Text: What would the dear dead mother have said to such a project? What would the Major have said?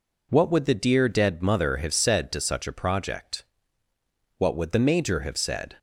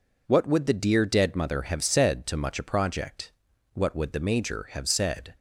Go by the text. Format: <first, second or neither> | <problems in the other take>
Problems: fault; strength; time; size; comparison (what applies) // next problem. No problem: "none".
first | says "much" for "such"; at 2.3 s